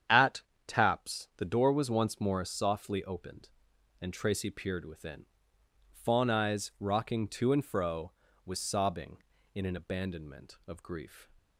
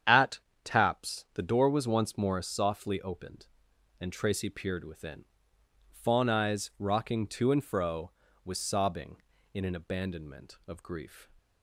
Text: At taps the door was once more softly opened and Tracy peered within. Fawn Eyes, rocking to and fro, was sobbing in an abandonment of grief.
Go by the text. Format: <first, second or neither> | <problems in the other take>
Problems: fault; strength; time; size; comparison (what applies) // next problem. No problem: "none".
neither | starts louder than the rest; strong; the same in both // pauses between "At" and "taps"; slight; the same in both